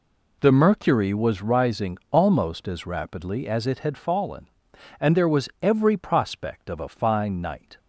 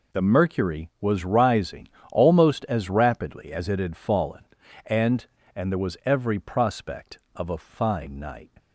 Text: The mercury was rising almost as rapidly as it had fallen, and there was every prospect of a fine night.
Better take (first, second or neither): first